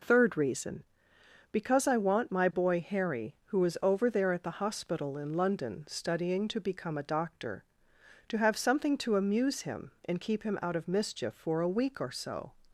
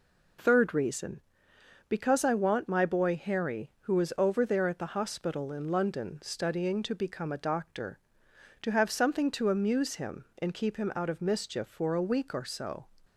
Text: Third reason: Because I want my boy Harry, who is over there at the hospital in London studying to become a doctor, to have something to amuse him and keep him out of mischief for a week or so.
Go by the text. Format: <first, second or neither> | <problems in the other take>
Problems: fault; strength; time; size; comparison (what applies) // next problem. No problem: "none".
neither | none